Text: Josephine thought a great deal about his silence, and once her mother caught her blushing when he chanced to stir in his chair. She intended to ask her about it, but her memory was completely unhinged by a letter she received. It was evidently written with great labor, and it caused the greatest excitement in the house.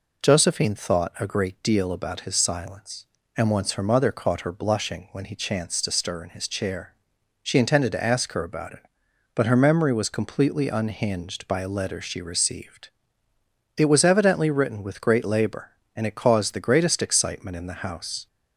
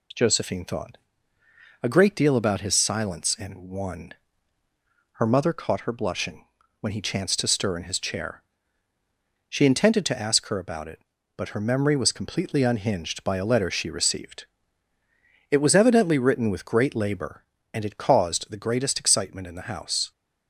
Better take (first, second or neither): first